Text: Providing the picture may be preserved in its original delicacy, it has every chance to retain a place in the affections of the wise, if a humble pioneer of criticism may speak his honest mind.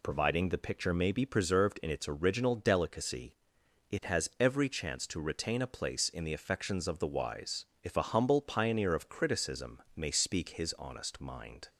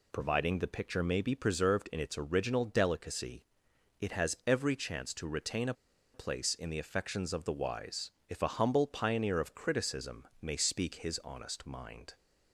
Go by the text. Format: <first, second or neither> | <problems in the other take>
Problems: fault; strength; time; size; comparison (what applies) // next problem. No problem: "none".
first | pauses between "a" and "place"; at 5.7 s; 0.41 s long // pauses between "criticism" and "may"; slight; at 10.2 s; 0.16 s long; slight in the first